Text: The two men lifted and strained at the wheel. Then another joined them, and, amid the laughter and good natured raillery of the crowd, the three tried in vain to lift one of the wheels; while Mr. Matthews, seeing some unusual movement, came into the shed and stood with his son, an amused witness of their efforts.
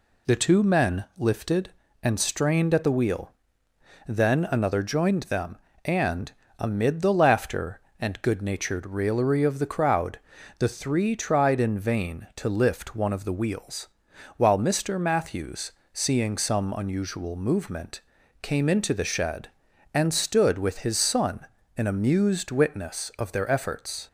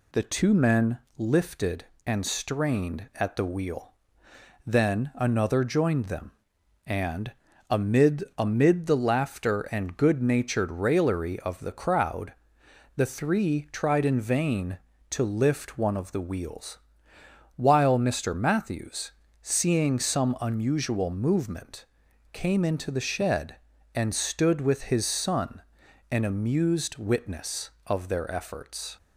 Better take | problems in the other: first | pauses between "men" and "lifted"; slight; at 0.9 s; 0.22 s long // says "amid" twice; at 8.3 s

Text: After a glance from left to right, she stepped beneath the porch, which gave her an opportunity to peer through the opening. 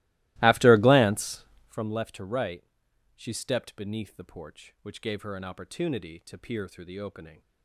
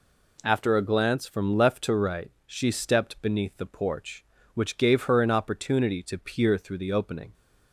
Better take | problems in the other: second | starts louder than the rest; strong; until 1.9 s; 18.5 dB

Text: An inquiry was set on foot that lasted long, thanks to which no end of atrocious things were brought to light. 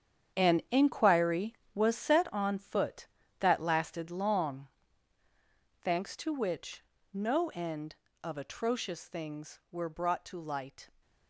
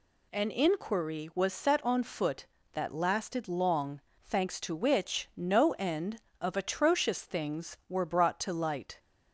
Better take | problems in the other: second | gets quieter; strong; throughout; 12.5 dB // pauses between "which" and "no"; slight; at 6.8 s; 0.30 s long

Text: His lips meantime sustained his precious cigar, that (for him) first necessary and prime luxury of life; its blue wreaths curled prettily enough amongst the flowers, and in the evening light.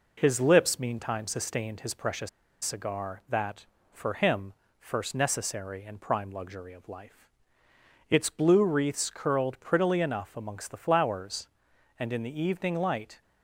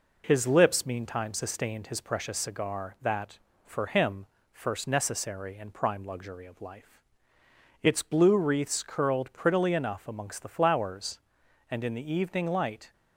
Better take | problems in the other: second | pauses between "precious" and "cigar"; slight; at 2.2 s; 0.35 s long

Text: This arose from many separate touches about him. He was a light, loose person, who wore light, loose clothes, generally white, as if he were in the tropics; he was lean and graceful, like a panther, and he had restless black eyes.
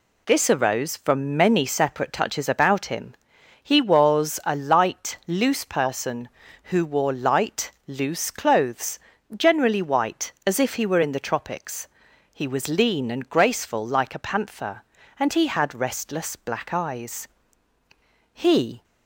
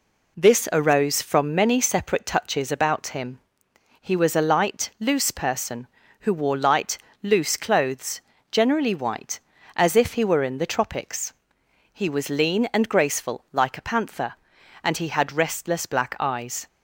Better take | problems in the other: second | goes on to say "He"; from 18.3 s on; 0.50 s long

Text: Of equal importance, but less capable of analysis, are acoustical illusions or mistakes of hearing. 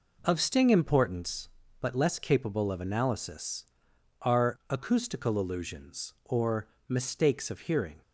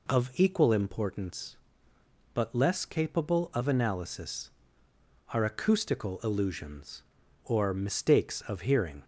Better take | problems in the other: second | says "sting" for "equal"; at 0.3 s // pauses between "or" and "mistakes"; slight; at 6.6 s; 0.22 s long

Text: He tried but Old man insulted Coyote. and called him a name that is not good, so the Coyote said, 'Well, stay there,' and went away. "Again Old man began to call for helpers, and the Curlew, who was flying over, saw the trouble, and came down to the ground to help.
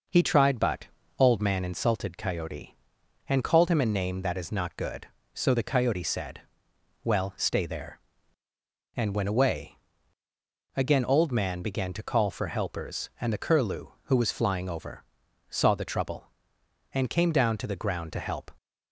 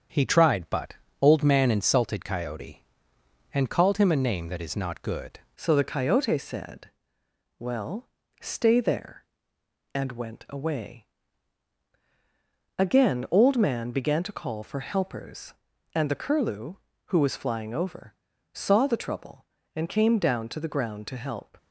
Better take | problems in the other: first | starts louder than the rest; strong; until 1.4 s; 7.5 dB // pauses between "but" and "Old"; slight; at 0.9 s; 0.26 s long; slight in the first // changes voice at "so"; from 5.5 s on; 16.0 s long

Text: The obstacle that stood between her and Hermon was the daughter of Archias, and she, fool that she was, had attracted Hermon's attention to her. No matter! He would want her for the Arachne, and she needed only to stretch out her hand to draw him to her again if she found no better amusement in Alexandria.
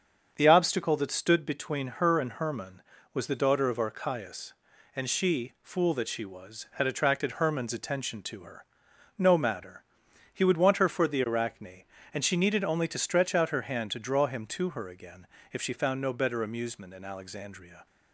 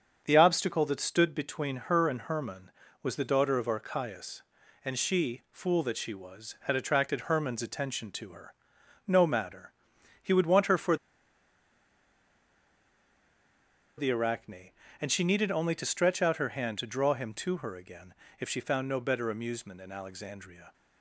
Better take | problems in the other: first | starts louder than the rest; strong; until 1.2 s; 7 dB; strong in the first // pauses between "for" and "the"; strong; at 10.9 s; 3.0 s long // pauses between "again" and "if"; slight; at 18.1 s; 0.24 s long; slight in the first

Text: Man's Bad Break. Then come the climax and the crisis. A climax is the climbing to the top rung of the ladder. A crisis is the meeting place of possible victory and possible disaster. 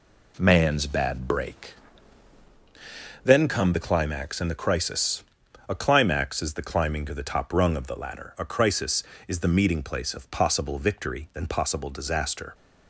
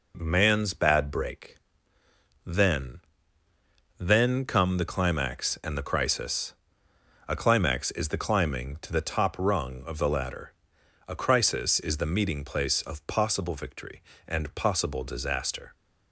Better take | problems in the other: first | says "Then" twice; at 3.9 s

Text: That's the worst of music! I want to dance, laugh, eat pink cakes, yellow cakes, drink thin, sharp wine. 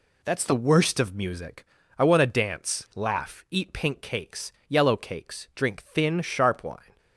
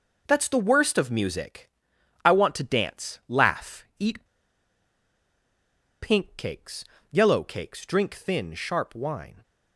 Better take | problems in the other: first | pauses between "eat" and "pink"; strong; at 4.2 s; 1.7 s long

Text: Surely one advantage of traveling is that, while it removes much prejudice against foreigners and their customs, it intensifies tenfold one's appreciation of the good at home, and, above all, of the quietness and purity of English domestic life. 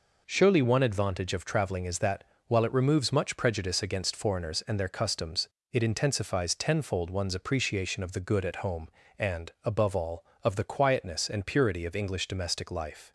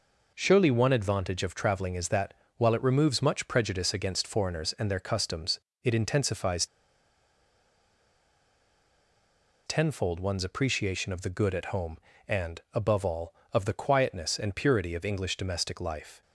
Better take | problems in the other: first | pauses between "intensifies" and "tenfold"; strong; at 6.6 s; 3.0 s long

